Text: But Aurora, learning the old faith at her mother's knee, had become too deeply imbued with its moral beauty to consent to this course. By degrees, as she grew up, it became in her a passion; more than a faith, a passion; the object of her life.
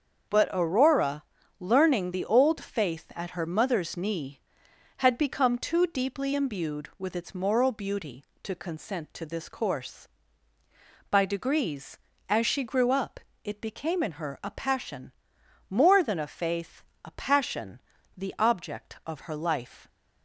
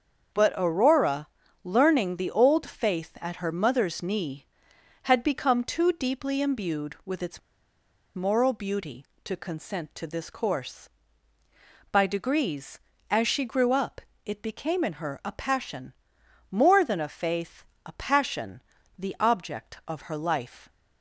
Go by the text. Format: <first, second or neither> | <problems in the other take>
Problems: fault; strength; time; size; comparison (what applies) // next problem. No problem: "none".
first | starts louder than the rest; until 1.7 s; 7 dB; also in the first // pauses between "its" and "moral"; noticeable; at 7.4 s; 0.74 s long